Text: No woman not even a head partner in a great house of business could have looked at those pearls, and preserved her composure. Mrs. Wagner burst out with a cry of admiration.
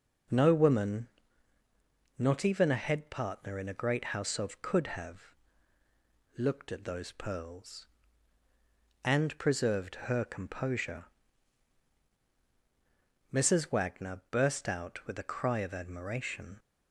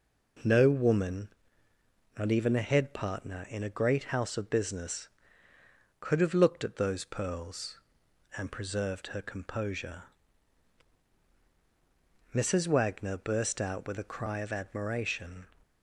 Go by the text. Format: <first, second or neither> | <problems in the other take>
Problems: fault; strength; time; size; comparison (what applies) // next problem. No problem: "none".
second | pauses between "woman" and "not"; at 1.0 s; 1.1 s long; noticeable in the second // skips "business"; at 4.6 s // pauses between "have" and "looked"; at 5.3 s; 1.0 s long